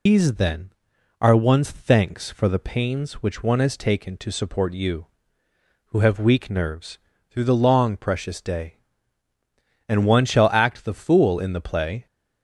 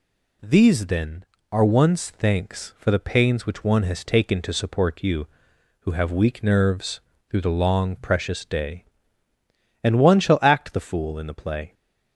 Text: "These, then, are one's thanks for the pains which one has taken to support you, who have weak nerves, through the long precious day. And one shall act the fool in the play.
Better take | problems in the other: second | loses the start of "These"; at 0.0 s; 115 ms

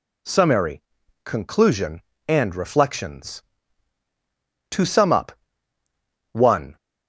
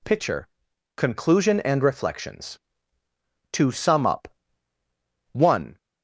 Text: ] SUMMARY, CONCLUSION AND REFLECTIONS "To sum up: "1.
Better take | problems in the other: first | says "Pitcher" for "SUMMARY"; at 0.0 s

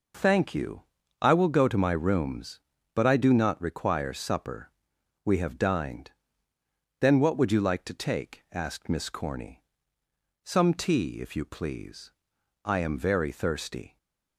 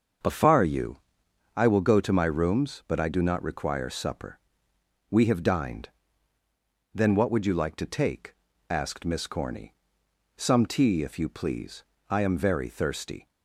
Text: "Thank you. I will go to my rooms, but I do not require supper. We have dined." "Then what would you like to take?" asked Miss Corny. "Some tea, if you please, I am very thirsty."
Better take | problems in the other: first | starts louder than the rest; until 1.8 s; 6.5 dB // says "Afar" for "Thank"; at 0.2 s

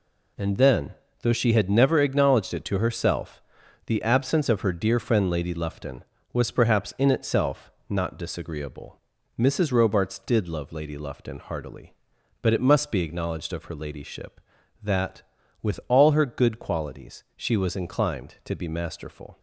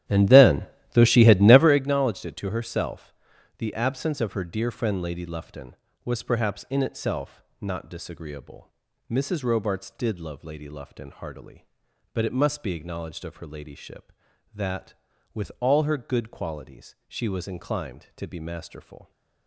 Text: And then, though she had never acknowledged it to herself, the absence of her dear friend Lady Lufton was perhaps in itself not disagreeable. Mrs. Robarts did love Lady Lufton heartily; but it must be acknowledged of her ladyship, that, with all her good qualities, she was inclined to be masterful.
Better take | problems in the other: first | starts louder than the rest; strong; until 1.9 s; 12 dB // pauses between "itself" and "not"; slight; at 7.4 s; 0.18 s long; slight in the first

